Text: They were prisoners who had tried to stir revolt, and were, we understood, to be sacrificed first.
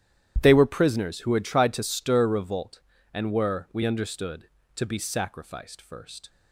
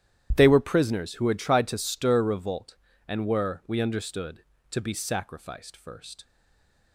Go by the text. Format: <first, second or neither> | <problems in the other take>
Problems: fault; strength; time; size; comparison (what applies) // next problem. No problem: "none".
first | starts louder than the rest; strong; until 1.3 s; 11 dB; strong in the first // stays silent after the last word; slight; from 6.2 s on; 0.7 s long